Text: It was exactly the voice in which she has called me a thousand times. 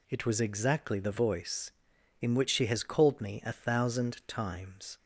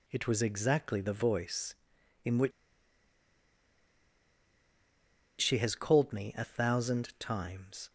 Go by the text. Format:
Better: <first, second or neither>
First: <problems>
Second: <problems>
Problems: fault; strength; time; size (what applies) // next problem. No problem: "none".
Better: first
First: none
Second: pauses between "which" and "she"; strong; at 2.5 s; 2.9 s long